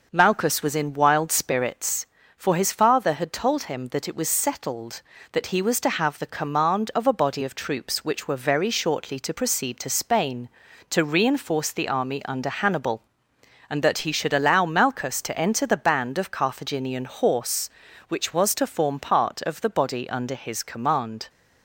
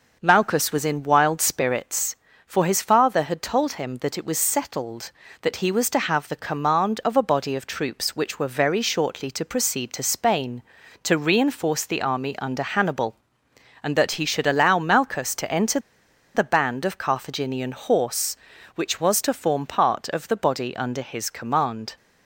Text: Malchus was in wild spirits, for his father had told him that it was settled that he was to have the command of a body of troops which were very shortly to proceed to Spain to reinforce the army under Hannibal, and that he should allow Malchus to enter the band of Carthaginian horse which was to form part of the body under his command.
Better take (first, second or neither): first